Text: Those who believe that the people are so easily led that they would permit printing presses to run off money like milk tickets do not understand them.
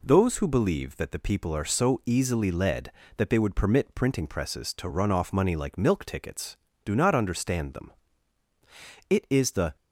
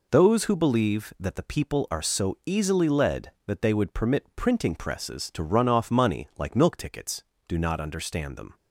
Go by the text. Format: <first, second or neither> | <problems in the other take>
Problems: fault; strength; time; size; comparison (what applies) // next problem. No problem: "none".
second | goes on to say "It is the"; noticeable; from 9.0 s on; 0.66 s long